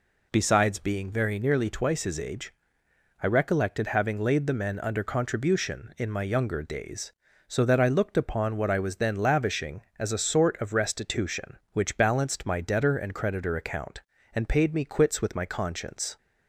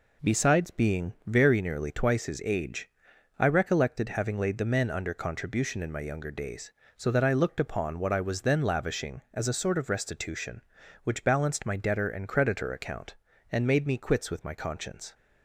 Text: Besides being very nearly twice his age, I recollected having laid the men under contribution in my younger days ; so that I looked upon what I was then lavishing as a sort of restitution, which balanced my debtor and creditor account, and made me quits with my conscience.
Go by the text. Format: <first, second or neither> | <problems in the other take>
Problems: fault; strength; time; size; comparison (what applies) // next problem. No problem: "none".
second | says "paid" for "made"; at 14.4 s